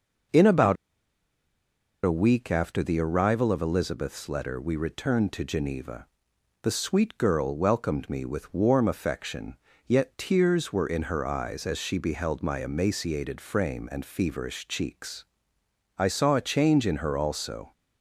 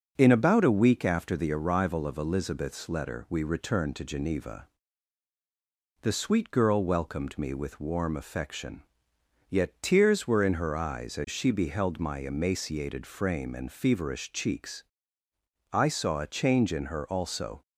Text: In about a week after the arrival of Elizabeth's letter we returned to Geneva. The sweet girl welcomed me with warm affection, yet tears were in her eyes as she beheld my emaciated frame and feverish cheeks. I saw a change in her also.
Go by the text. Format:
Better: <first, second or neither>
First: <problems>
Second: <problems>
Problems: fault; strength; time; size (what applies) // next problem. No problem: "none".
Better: second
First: starts louder than the rest; noticeable; until 2.6 s; 6 dB // pauses between "about" and "a"; strong; at 0.7 s; 1.2 s long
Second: starts louder than the rest; until 1.1 s; 6 dB